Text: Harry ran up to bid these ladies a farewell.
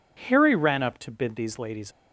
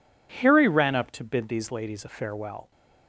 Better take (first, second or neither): second